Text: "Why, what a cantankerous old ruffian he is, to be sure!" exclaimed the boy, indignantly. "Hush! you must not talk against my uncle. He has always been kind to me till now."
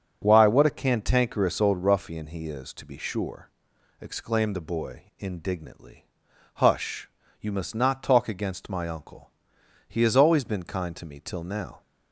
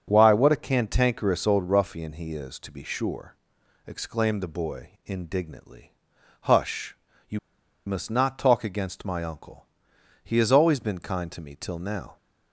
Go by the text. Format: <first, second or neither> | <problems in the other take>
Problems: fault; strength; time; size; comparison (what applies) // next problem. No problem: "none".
first | starts louder than the rest; until 1.0 s; 6.5 dB; also in the first // pauses between "you" and "must"; noticeable; at 7.3 s; 0.47 s long